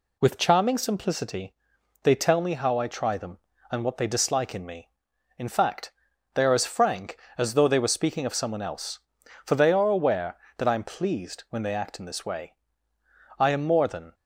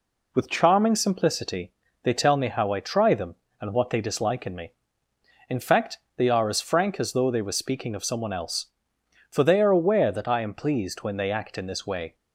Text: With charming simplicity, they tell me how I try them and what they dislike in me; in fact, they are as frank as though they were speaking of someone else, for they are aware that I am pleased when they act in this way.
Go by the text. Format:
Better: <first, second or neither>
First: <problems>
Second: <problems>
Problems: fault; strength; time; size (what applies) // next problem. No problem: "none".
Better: second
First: goes on to say "I am more than"; noticeable; from 13.3 s on; 0.78 s long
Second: none